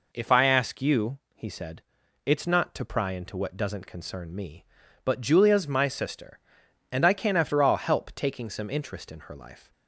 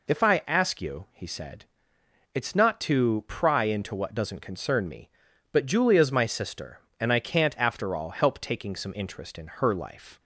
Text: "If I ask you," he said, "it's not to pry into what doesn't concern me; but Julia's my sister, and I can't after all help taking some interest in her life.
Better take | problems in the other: second | says "can" for "can't"; at 7.1 s

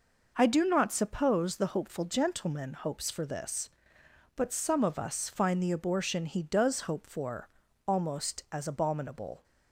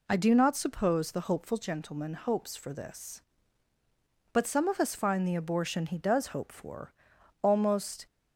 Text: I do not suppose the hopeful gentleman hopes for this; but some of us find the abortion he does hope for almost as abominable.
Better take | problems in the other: first | pauses between "for" and "almost"; noticeable; at 6.9 s; 0.50 s long; also in the first // stops before "as abominable"; at 8.0 s

